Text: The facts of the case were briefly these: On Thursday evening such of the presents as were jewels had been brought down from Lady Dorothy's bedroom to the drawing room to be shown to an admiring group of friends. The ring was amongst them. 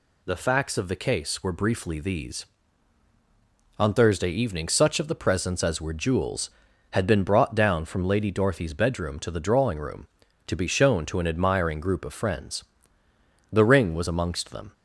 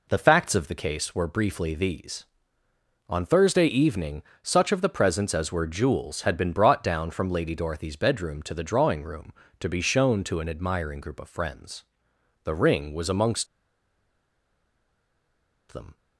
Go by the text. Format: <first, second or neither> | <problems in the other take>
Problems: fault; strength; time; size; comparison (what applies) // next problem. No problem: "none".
first | pauses between "evening" and "such"; slight; at 4.2 s; 0.18 s long // pauses between "amongst" and "them"; strong; at 13.4 s; 2.2 s long